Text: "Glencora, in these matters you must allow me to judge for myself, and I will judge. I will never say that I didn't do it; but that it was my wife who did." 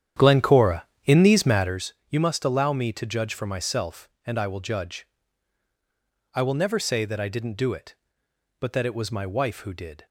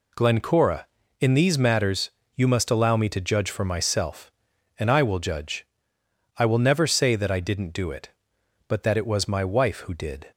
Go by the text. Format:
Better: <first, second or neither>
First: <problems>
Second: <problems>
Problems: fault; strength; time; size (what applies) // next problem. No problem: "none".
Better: second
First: starts louder than the rest; strong; until 1.9 s; 10 dB // pauses between "matters" and "you"; slight; at 1.9 s; 0.16 s long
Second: pauses between "matters" and "you"; slight; at 2.1 s; 0.24 s long